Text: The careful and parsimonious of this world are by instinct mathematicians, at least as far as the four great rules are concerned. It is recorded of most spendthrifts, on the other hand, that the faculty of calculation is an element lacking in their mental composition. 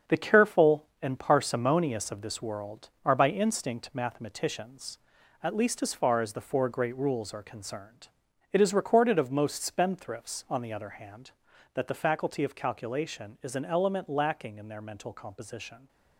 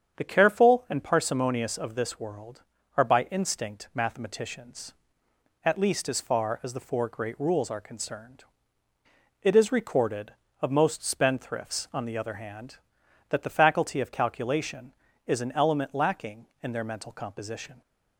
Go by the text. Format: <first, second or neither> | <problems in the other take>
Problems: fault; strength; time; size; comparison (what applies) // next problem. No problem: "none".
second | gets quieter; strong; throughout; 7.5 dB // starts louder than the rest; until 1.2 s; 7 dB; strong in the second